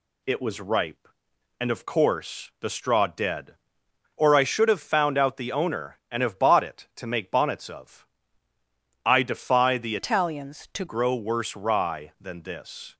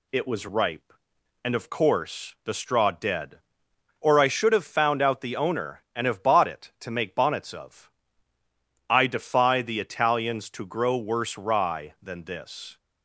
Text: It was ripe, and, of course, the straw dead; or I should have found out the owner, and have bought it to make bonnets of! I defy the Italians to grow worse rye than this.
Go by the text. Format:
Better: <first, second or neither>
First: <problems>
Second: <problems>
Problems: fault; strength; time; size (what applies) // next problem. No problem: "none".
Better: second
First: changes voice from "Italians" to "to"; from 9.9 to 10.8 s; 0.9 s long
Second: none